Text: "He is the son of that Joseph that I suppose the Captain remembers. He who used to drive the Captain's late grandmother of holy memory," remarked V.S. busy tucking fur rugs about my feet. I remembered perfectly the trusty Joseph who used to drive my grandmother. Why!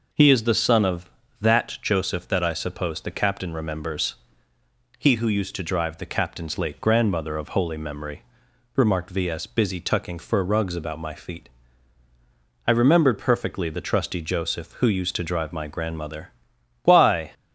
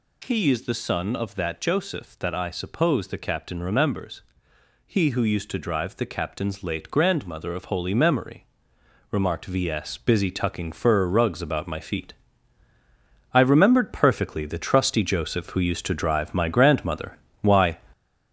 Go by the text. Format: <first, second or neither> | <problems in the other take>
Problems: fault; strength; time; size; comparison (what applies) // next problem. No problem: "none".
first | gets louder; noticeable; throughout; 5 dB